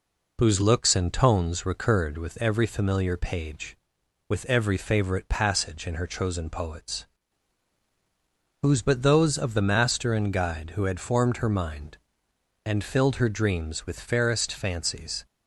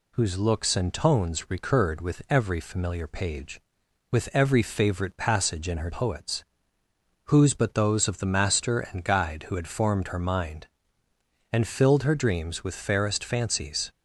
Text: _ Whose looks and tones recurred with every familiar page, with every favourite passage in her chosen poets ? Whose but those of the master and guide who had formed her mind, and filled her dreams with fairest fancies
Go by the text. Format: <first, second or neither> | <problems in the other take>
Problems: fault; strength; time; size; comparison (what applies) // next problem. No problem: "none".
first | skips "chosen"; at 5.8 s